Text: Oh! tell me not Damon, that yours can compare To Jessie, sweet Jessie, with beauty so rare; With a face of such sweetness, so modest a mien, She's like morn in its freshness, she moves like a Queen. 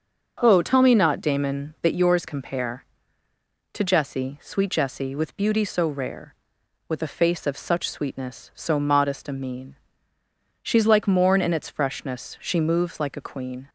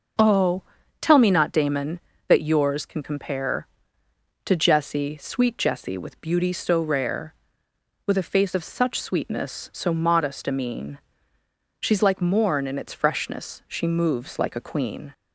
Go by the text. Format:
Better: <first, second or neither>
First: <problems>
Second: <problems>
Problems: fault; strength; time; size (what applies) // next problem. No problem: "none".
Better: second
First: starts louder than the rest; until 1.4 s; 6.5 dB // skips "can"; at 2.2 s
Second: none